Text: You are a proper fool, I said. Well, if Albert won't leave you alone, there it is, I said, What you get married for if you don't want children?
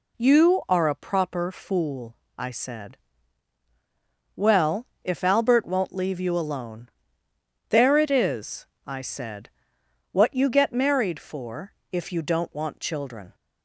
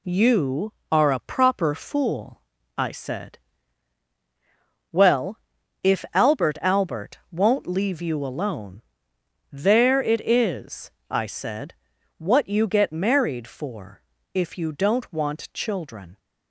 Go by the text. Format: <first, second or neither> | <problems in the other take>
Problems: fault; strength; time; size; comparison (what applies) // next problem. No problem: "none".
first | says "Albert" twice; at 6.5 s // pauses between "for" and "if"; slight; at 14.0 s; 0.32 s long; slight in the first